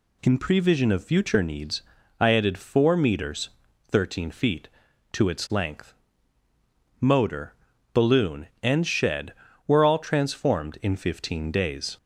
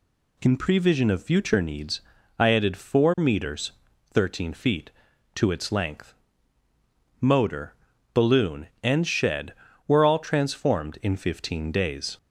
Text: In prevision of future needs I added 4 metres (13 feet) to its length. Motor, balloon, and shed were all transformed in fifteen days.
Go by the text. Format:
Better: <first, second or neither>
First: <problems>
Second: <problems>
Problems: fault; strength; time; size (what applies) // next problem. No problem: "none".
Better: neither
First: pauses between "needs" and "I"; slight; at 1.8 s; 0.36 s long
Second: pauses between "needs" and "I"; slight; at 2.0 s; 0.36 s long